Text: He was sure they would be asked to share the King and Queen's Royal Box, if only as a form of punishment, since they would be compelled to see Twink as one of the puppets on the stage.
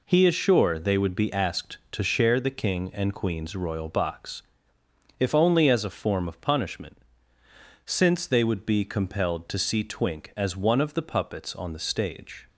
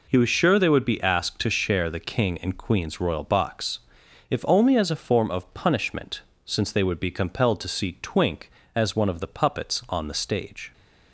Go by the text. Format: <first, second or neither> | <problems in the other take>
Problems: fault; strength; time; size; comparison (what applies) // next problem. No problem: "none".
second | says "is" for "was"; at 0.2 s